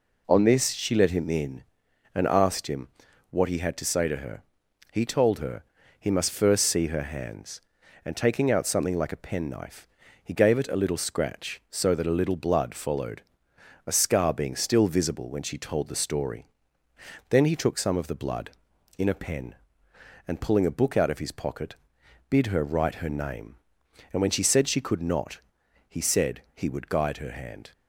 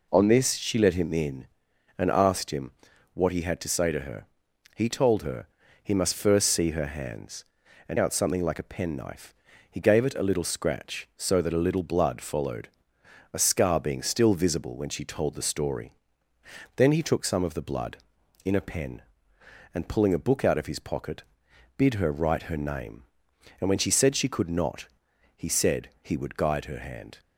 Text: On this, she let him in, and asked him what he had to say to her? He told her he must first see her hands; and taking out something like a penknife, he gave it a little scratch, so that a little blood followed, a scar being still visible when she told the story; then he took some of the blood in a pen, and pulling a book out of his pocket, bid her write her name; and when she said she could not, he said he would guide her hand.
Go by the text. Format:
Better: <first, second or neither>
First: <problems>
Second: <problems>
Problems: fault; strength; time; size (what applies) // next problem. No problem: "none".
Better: first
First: pauses between "him" and "what"; at 2.8 s; 0.42 s long // pauses between "her" and "he"; slight; at 5.6 s; 0.36 s long // pauses between "said" and "he"; slight; at 26.3 s; 0.16 s long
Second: pauses between "him" and "what"; at 2.7 s; 0.42 s long // pauses between "her" and "he"; slight; at 5.4 s; 0.36 s long // skips "taking"; at 7.9 s // pauses between "said" and "he"; slight; at 25.8 s; 0.16 s long